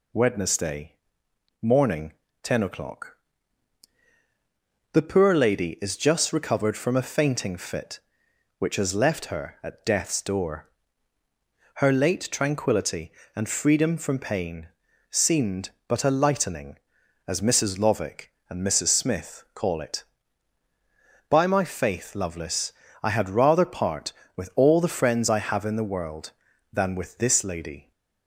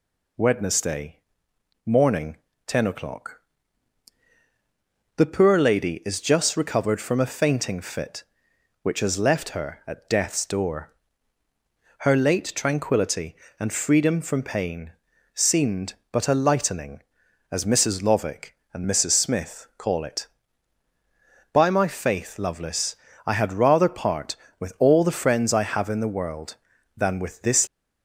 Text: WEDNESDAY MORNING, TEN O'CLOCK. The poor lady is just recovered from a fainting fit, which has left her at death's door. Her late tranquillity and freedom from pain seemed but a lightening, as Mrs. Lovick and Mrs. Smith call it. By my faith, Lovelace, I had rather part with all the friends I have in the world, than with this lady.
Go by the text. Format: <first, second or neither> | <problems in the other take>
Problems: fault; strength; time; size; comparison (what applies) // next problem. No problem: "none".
first | pauses between "WEDNESDAY" and "MORNING"; noticeable; at 1.1 s; 0.66 s long; noticeable in the first // pauses between "pain" and "seemed"; at 14.9 s; 0.42 s long; also in the first // stops before "lady"; at 27.6 s